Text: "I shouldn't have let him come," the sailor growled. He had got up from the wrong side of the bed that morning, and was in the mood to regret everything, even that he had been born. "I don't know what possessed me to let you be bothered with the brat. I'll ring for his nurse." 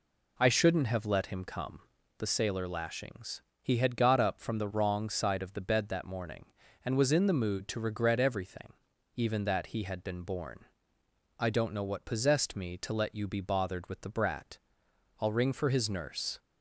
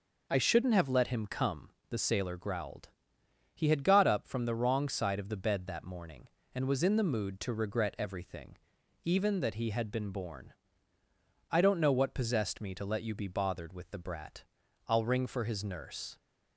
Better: second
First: says "lashings" for "growled"; at 2.6 s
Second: none

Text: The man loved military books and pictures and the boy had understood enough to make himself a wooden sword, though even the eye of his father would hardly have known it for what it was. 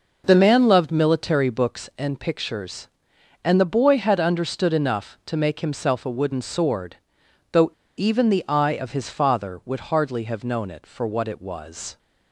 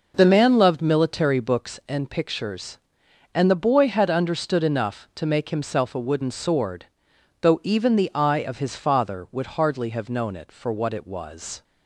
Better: second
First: pauses between "though" and "even"; slight; at 7.6 s; 0.28 s long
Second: none

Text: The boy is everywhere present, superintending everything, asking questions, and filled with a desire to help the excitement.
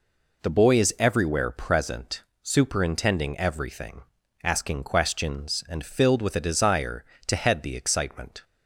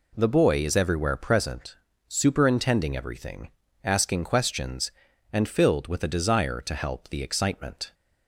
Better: second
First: says "head" for "help"; at 7.3 s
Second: none

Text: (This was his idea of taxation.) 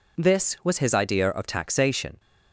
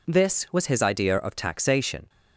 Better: neither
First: none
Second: none

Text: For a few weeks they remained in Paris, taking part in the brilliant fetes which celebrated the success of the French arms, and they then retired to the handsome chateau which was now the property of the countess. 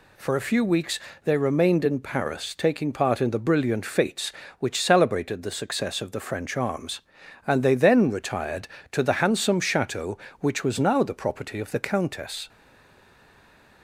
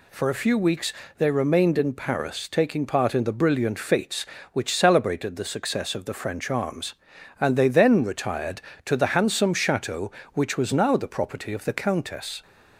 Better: second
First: pauses between "weeks" and "they"; slight; at 0.9 s; 0.26 s long // stays silent after the last word; noticeable; from 12.4 s on; 1.4 s long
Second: pauses between "weeks" and "they"; slight; at 0.9 s; 0.26 s long

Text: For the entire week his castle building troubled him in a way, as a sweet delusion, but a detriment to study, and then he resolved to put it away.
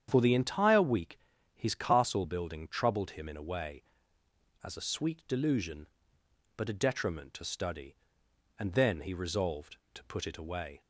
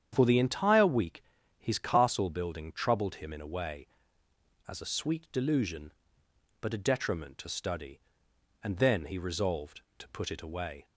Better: neither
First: starts louder than the rest; strong; until 1.1 s; 8.5 dB // pauses between "week" and "his"; slight; at 1.1 s; 0.34 s long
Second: starts louder than the rest; strong; until 1.1 s; 8.5 dB // pauses between "week" and "his"; slight; at 1.2 s; 0.33 s long

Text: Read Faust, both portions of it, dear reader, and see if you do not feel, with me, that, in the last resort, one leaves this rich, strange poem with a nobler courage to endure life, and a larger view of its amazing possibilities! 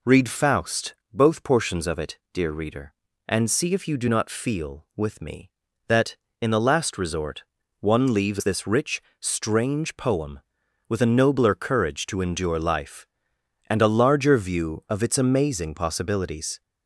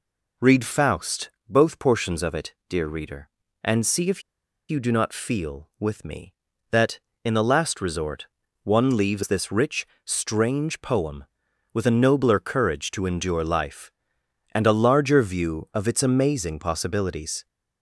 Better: first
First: none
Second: pauses between "if" and "you"; noticeable; at 4.2 s; 0.47 s long

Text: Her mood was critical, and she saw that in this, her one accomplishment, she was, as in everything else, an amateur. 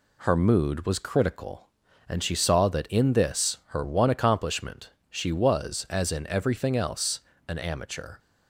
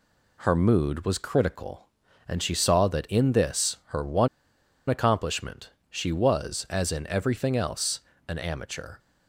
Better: first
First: none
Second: pauses between "one" and "accomplishment"; noticeable; at 4.2 s; 0.62 s long

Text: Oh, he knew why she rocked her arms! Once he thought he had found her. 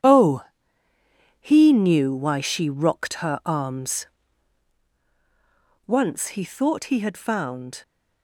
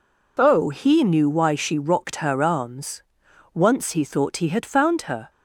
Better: second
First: stops before "her"; at 7.8 s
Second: none

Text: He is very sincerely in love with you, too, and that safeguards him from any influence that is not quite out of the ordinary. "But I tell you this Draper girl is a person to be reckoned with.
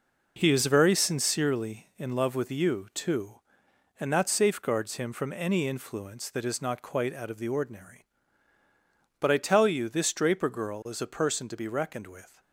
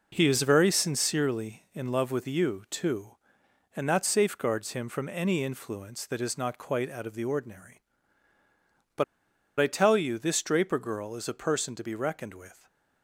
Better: first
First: none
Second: pauses between "But" and "I"; noticeable; at 9.0 s; 0.56 s long

